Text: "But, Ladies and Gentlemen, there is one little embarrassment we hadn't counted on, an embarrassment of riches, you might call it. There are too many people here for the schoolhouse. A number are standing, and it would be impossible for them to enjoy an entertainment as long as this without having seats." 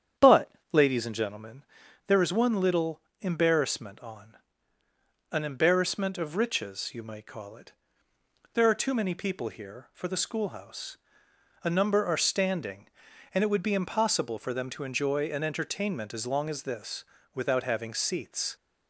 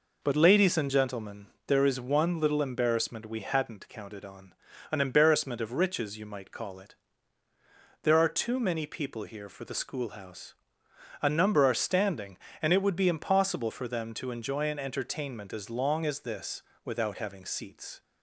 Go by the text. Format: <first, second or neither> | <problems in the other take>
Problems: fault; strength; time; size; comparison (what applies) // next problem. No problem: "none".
second | starts louder than the rest; strong; until 1.4 s; 8.5 dB // pauses between "little" and "embarrassment"; slight; at 3.0 s; 0.20 s long // skips "we hadn't counted"; at 3.9 s // pauses between "this" and "without"; slight; at 17.0 s; 0.30 s long; slight in the second